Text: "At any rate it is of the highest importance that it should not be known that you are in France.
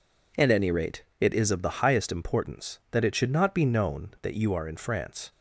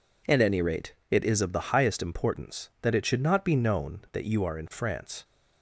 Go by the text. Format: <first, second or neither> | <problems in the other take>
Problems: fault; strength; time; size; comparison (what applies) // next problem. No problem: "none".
neither | pauses between "rate" and "it"; slight; the same in both